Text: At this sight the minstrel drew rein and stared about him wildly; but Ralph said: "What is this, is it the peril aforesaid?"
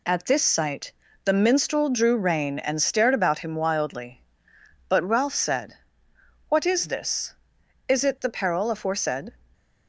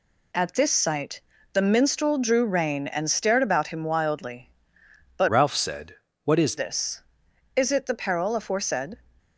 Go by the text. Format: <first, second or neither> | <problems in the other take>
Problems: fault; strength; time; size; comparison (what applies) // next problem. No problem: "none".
first | pauses between "sight" and "the"; slight; at 1.2 s; 0.32 s long; slight in the first // changes voice from "Ralph" to "is"; from 5.2 to 6.5 s; 1.3 s long